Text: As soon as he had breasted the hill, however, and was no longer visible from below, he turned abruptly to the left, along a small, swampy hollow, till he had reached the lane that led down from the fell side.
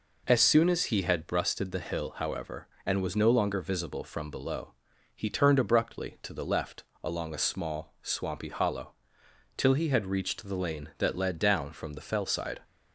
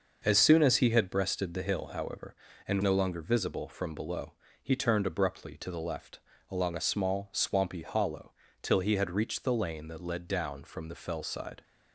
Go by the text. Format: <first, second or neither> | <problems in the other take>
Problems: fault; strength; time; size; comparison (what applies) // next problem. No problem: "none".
first | starts louder than the rest; noticeable; until 1.2 s; 6 dB // skips "was"; at 2.8 s